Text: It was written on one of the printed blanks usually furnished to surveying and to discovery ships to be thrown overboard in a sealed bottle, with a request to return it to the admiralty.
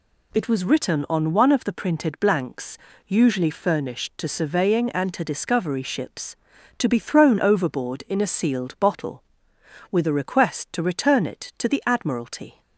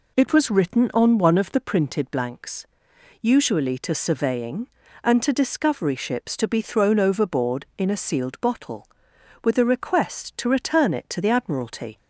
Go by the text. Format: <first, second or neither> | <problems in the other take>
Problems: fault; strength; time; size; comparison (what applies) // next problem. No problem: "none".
first | pauses between "blanks" and "usually"; noticeable; at 2.6 s; 0.54 s long; slight in the first // skips "furnished"; at 3.7 s